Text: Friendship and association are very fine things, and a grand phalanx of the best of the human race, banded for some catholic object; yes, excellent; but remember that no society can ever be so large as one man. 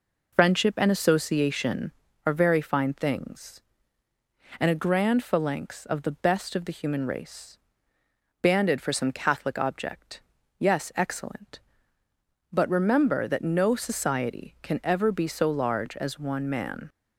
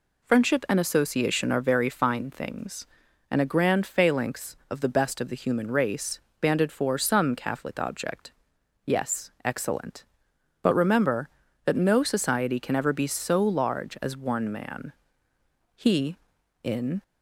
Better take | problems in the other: first | goes on to say "He in"; noticeable; from 15.7 s on; 1.2 s long

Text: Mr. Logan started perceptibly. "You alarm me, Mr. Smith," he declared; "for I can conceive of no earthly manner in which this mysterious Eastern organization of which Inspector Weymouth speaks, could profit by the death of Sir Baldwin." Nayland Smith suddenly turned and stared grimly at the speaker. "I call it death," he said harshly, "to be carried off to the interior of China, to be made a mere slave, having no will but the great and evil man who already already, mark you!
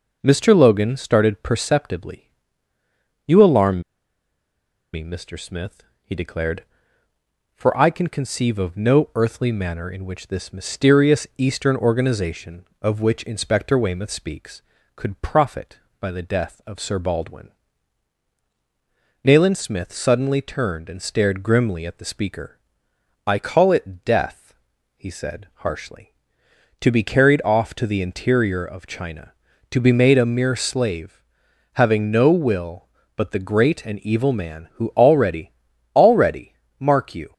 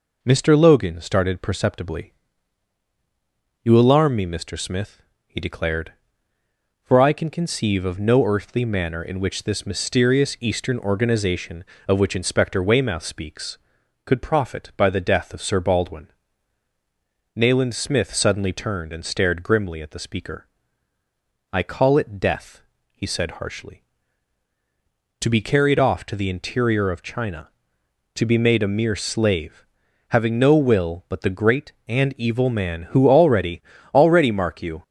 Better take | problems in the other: second | pauses between "alarm" and "me"; at 3.8 s; 1.1 s long // pauses between "already" and "already"; at 35.5 s; 0.42 s long; slight in the second

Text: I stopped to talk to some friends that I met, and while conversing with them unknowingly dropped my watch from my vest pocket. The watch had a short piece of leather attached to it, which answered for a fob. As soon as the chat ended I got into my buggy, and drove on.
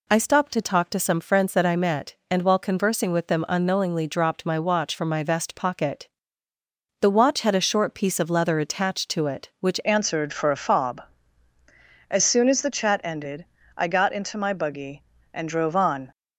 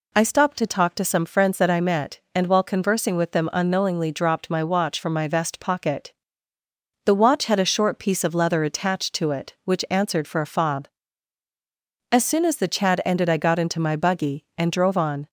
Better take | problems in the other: second | changes voice at "answered"; from 9.8 s on; 6.3 s long // pauses between "ended" and "I"; slight; at 13.4 s; 0.32 s long

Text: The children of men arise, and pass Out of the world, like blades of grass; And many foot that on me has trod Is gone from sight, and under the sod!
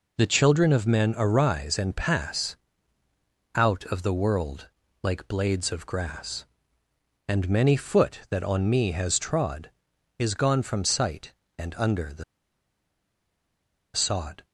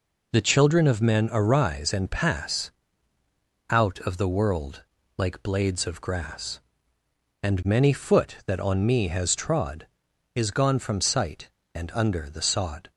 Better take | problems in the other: second | pauses between "pass" and "Out"; noticeable; at 2.5 s; 0.98 s long; noticeable in the second // pauses between "the" and "sod"; strong; at 12.2 s; 1.7 s long

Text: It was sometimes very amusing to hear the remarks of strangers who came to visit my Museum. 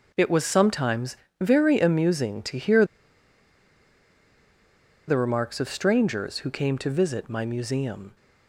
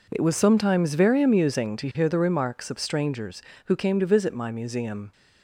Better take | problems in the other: second | pauses between "sometimes" and "very"; slight; at 1.1 s; 0.24 s long // pauses between "hear" and "the"; strong; at 2.8 s; 2.2 s long

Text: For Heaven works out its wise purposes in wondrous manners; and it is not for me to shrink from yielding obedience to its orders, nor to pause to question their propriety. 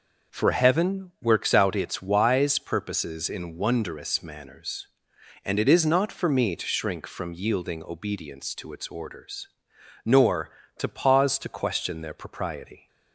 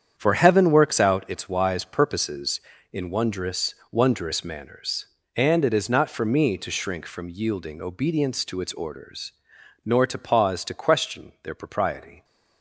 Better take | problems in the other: first | starts louder than the rest; strong; until 1.1 s; 8.5 dB // says "wondrous" twice; at 3.9 s

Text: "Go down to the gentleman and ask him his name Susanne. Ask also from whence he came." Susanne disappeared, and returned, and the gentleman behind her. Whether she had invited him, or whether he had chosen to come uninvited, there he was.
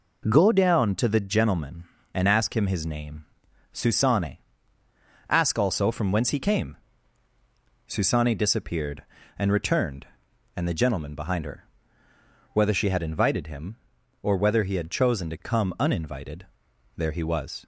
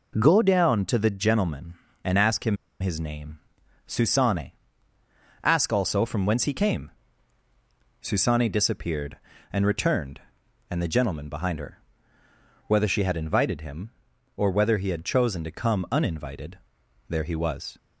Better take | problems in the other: first | pauses between "him" and "his"; slight; at 2.5 s; 0.25 s long // pauses between "name" and "Susanne"; noticeable; at 3.3 s; 0.48 s long; noticeable in the first

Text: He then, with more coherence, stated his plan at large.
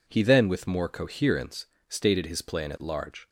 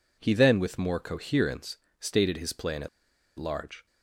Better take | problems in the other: first | pauses between "at" and "large"; noticeable; at 2.8 s; 0.50 s long

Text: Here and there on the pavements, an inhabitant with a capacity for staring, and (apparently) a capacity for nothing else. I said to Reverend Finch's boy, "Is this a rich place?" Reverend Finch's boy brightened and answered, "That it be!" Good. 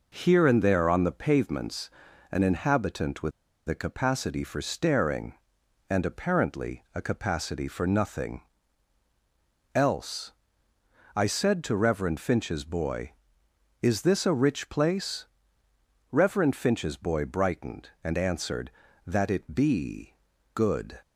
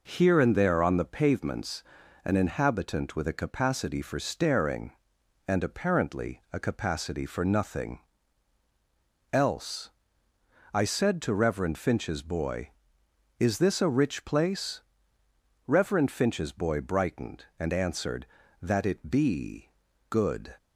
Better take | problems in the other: second | pauses between "with" and "a"; at 3.3 s; 0.36 s long // pauses between "nothing" and "else"; strong; at 8.4 s; 1.3 s long; strong in the second

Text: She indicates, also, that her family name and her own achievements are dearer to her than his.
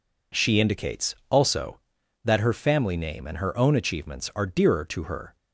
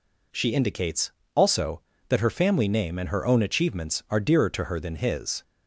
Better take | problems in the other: second | stops before "than his"; at 5.3 s

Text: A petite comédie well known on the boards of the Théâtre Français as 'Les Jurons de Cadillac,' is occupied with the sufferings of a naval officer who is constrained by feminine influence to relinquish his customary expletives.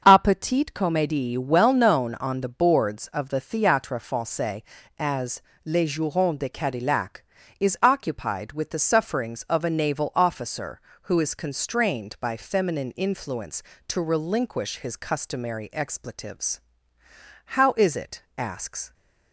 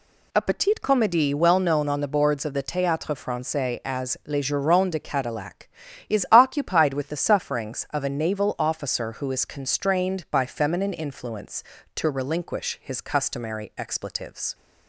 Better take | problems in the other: second | starts louder than the rest; until 1.0 s; 6.5 dB // pauses between "as" and "Les"; slight; at 5.4 s; 0.22 s long // goes on to say "How is it asks"; from 17.4 s on; 1.4 s long

